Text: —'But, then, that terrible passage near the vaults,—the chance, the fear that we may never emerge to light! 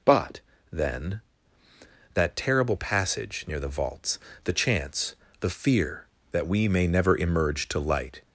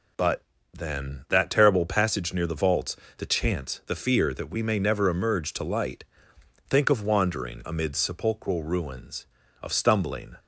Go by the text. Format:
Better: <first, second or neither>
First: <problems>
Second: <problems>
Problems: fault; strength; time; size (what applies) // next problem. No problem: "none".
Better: first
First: none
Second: goes on to say "Think of wandering amid sepulchral ruins of stumbling"; strong; from 6.6 s on; 3.6 s long